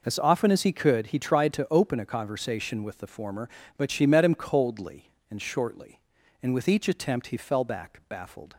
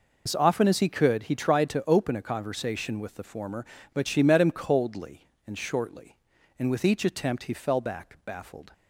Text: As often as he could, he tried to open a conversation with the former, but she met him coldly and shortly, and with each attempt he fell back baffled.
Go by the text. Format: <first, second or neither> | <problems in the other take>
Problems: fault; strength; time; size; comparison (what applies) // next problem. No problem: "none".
first | loses the start of "As"; at 0.2 s; 50 ms